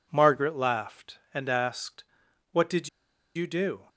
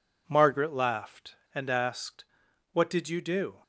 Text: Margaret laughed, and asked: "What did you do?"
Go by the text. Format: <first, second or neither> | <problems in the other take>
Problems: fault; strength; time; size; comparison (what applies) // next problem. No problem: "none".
second | pauses between "did" and "you"; noticeable; at 2.8 s; 0.47 s long